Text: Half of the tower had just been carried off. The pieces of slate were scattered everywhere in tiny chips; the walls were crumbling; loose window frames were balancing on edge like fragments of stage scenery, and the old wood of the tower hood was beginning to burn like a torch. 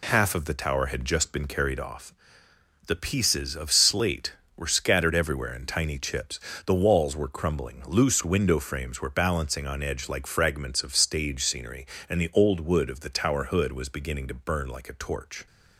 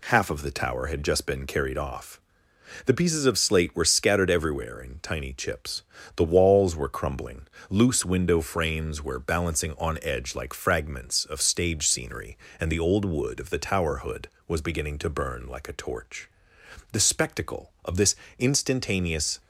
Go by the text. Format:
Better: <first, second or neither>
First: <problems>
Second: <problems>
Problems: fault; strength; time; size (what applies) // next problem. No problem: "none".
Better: first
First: none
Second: goes on to say "The spectacle of this instantaneous"; strong; from 16.9 s on; 2.4 s long